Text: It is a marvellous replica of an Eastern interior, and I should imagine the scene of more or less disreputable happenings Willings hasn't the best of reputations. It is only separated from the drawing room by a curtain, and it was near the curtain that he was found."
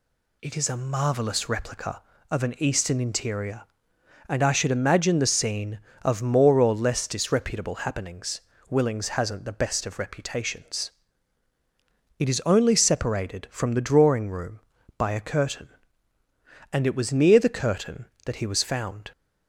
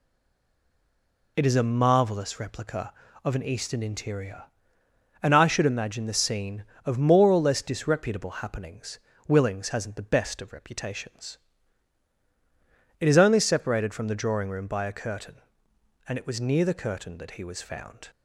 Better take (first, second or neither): first